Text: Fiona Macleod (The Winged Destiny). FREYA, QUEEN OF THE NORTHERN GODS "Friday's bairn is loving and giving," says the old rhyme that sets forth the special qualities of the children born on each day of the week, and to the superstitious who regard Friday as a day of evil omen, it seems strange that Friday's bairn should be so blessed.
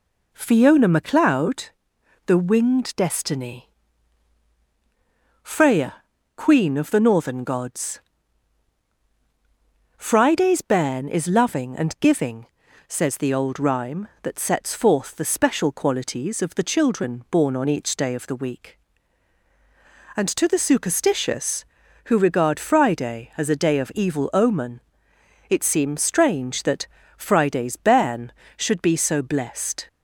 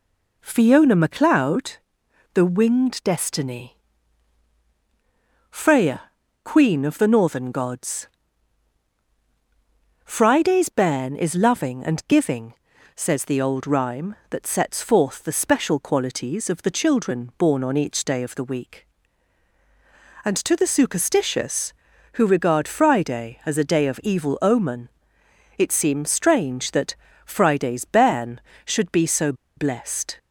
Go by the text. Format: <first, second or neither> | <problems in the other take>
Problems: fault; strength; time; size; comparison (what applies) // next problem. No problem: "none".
first | pauses between "GODS" and "Friday's"; strong; at 8.0 s; 1.9 s long; strong in the first // pauses between "that" and "Friday's"; slight; at 26.9 s; 0.30 s long; slight in the first // pauses between "so" and "blessed"; slight; at 29.3 s; 0.23 s long